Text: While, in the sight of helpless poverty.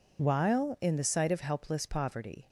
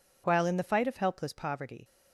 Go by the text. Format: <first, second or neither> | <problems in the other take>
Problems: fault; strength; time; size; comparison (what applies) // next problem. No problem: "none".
first | says "fight" for "sight"; at 0.6 s